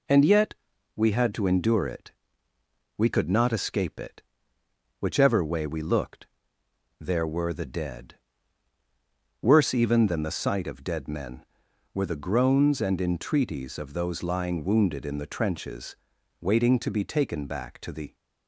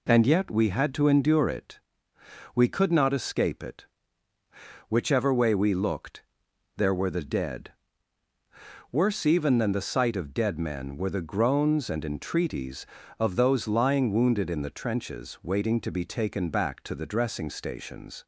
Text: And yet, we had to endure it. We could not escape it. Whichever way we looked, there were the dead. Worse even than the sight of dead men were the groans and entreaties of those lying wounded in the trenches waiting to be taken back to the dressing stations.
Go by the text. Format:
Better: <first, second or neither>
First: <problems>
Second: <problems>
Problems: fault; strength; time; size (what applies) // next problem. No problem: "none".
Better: second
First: pauses between "trenches" and "waiting"; noticeable; at 15.9 s; 0.46 s long // stops before "dressing stations"; at 18.1 s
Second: none